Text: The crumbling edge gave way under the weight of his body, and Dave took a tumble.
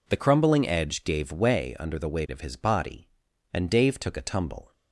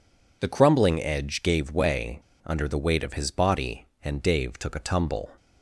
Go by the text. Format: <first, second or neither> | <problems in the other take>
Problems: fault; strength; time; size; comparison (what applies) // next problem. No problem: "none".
first | pauses between "way" and "under"; slight; at 2.2 s; 0.23 s long